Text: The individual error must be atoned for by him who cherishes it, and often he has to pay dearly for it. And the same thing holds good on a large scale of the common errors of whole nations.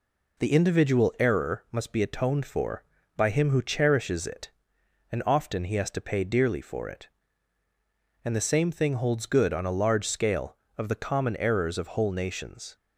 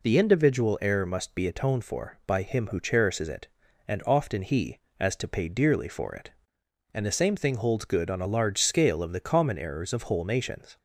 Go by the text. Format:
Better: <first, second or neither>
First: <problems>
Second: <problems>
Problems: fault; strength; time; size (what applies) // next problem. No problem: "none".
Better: first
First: none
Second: says "as" for "has"; at 4.9 s